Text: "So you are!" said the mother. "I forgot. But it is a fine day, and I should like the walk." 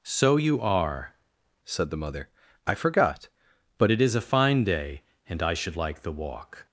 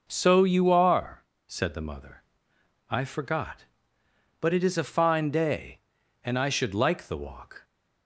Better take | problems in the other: second | changes voice from "said" to "But"; from 1.6 to 3.8 s; 2.2 s long

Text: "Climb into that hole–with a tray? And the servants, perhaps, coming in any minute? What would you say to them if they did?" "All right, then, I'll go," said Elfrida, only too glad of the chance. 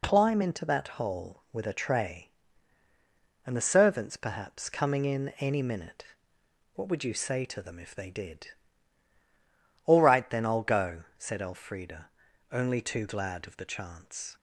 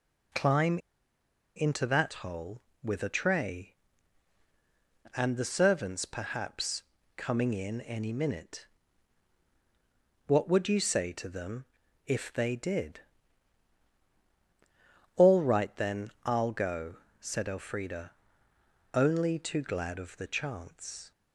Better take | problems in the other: first | pauses between "Climb" and "into"; noticeable; at 0.7 s; 0.77 s long // pauses between "them" and "if"; at 11.6 s; 0.40 s long

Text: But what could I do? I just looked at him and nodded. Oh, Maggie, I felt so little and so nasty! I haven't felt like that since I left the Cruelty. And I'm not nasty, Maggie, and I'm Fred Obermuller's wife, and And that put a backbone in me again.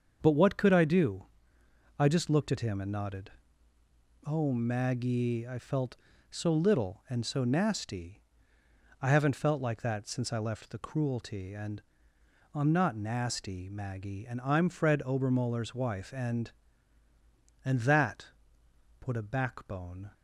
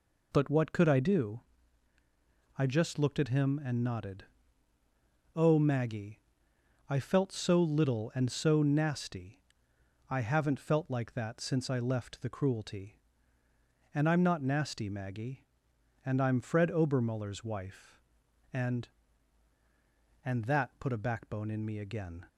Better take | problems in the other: second | starts louder than the rest; until 1.2 s; 6.5 dB // pauses between "And" and "I'm"; noticeable; at 11.8 s; 0.72 s long // pauses between "that" and "put"; noticeable; at 18.2 s; 0.72 s long // stops before "in me again"; at 20.1 s

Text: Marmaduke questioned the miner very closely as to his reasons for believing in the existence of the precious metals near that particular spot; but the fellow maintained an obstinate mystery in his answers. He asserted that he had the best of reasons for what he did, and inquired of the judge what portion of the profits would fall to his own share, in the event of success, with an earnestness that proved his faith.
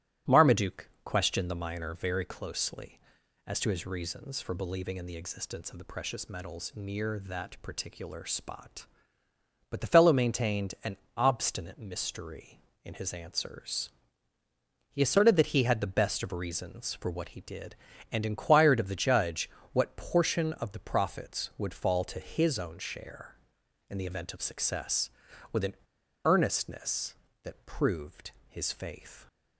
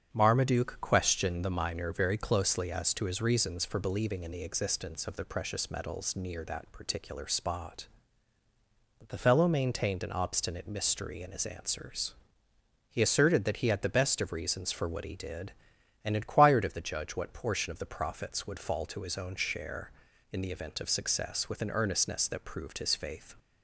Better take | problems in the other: second | starts louder than the rest; strong; until 1.4 s; 14 dB; strong in the second // pauses between "Marmaduke" and "questioned"; slight; at 0.8 s; 0.16 s long // pauses between "an" and "obstinate"; slight; at 10.9 s; 0.18 s long // pauses between "judge" and "what"; slight; at 19.4 s; 0.22 s long // pauses between "an" and "earnestness"; noticeable; at 25.7 s; 0.50 s long // pauses between "proved" and "his"; slight; at 28.3 s; 0.18 s long

